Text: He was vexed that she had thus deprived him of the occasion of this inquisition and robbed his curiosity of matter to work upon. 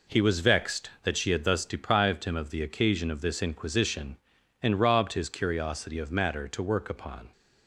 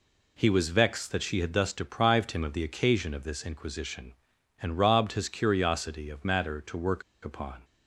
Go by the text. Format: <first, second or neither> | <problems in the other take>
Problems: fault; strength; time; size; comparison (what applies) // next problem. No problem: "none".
first | pauses between "work" and "upon"; slight; at 7.0 s; 0.21 s long